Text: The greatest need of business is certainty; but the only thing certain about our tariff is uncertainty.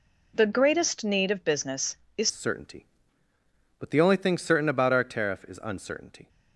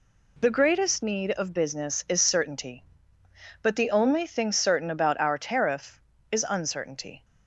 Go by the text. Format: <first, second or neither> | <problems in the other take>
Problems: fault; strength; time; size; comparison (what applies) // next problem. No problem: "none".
second | changes voice at "certainty"; from 2.3 s on; 3.9 s long